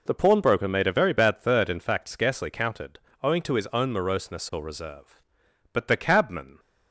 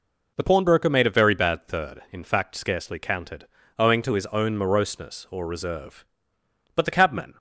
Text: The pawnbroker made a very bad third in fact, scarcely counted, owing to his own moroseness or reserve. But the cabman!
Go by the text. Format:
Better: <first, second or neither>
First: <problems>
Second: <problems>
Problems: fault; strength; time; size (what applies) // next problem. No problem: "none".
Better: neither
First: none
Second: none